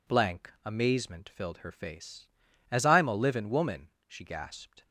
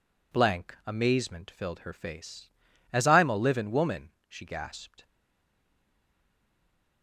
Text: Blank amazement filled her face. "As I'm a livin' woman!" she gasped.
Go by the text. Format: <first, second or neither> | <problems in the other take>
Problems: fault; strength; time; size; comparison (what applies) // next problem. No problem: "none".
first | stays silent after the last word; noticeable; from 5.0 s on; 2.0 s long